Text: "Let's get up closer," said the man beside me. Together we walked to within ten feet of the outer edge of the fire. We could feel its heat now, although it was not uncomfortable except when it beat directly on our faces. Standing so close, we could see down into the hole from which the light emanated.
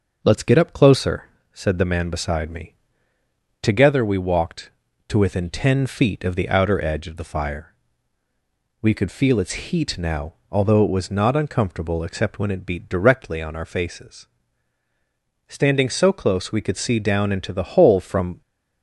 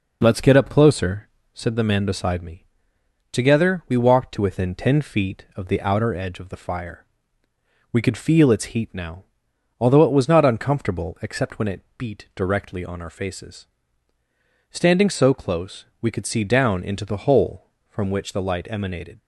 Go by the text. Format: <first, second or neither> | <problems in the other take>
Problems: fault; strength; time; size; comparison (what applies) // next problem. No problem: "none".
second | stops before "which the light emanated"; at 18.4 s